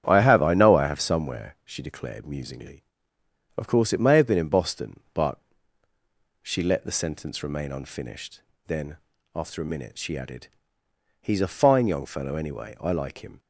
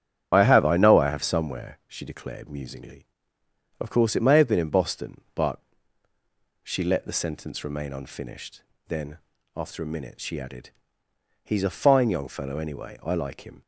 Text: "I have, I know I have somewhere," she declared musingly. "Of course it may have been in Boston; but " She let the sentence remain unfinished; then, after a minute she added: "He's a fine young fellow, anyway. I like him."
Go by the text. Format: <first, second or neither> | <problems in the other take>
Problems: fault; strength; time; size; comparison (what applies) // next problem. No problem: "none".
first | loses the start of "I"; at 0.3 s; 60 ms // starts louder than the rest; strong; until 1.3 s; 9.5 dB; strong in the first